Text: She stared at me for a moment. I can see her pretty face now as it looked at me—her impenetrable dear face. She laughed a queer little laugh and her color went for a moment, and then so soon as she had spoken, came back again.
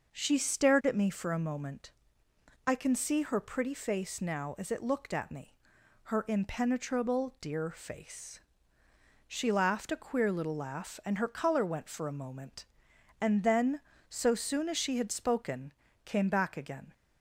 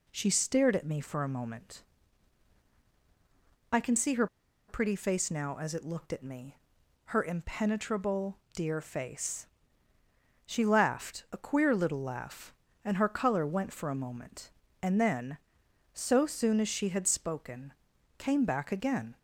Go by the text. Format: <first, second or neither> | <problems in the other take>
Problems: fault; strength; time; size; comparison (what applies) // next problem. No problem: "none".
first | pauses between "her" and "pretty"; at 4.2 s; 0.42 s long // pauses between "impenetrable" and "dear"; slight; at 8.3 s; 0.18 s long